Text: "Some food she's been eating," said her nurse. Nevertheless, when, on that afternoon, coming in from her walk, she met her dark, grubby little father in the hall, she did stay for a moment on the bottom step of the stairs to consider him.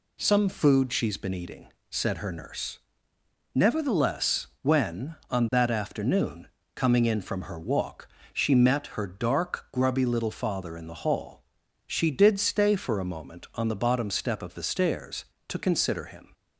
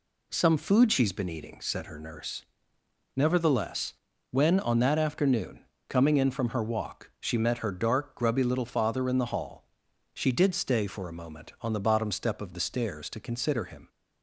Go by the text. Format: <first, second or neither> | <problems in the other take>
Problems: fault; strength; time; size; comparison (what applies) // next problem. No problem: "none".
neither | none